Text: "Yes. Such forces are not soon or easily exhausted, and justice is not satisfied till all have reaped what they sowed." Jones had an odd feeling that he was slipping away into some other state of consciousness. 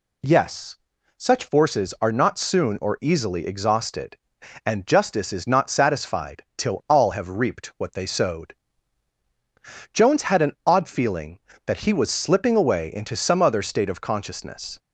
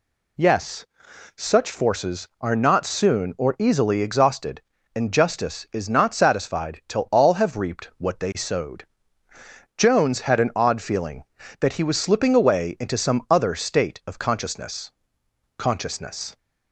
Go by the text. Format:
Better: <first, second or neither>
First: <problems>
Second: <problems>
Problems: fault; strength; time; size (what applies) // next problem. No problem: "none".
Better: first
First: none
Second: says "consciousness" twice; at 15.5 s